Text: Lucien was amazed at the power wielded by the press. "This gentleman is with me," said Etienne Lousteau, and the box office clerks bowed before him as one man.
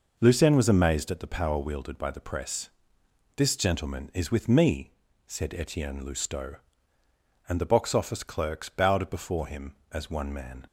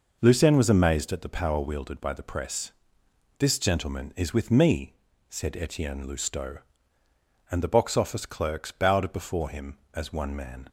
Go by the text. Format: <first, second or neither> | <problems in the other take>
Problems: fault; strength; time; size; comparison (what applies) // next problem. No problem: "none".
neither | none